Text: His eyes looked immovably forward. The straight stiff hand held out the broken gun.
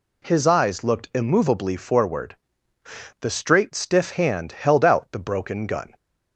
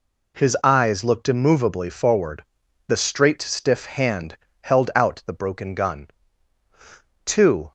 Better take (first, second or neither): first